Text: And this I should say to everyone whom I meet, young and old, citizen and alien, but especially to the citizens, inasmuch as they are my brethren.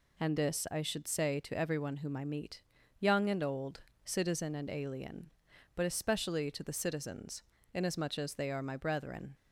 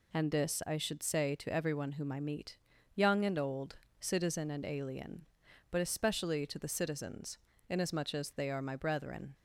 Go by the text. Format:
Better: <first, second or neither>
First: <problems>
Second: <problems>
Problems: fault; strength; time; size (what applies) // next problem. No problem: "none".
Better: neither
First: none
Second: none